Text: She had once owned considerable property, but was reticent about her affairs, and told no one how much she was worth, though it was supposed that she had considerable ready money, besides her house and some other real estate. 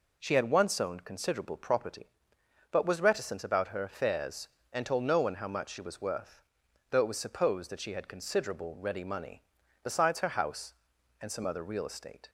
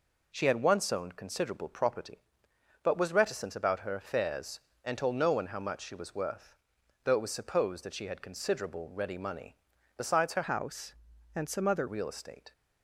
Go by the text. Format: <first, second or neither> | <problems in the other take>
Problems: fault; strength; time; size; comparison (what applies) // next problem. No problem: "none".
first | changes voice from "house" to "other"; from 10.4 to 11.8 s; 1.4 s long